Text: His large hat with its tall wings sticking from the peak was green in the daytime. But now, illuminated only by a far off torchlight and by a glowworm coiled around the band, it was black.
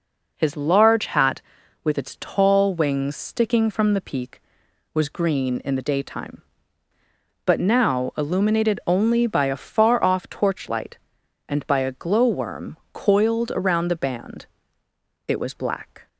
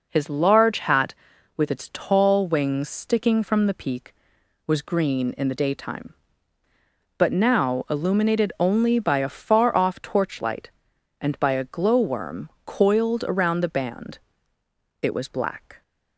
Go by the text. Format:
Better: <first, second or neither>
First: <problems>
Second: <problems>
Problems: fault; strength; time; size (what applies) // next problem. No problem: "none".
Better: neither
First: pauses between "glowworm" and "coiled"; slight; at 12.7 s; 0.16 s long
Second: pauses between "glowworm" and "coiled"; slight; at 12.4 s; 0.16 s long